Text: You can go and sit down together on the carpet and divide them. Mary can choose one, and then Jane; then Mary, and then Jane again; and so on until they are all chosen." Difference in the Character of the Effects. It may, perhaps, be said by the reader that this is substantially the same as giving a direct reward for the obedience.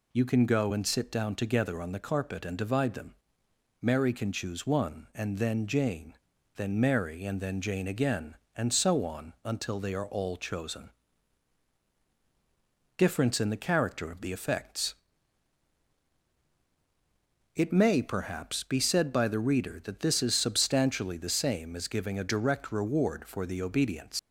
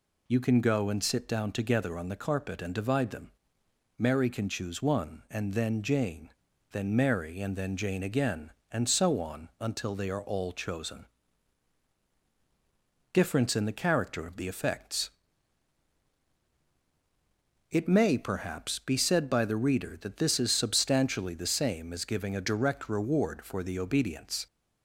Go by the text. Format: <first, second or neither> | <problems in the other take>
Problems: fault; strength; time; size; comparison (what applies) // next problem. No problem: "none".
second | leaves "obedience" unfinished; at 24.1 s; 100 ms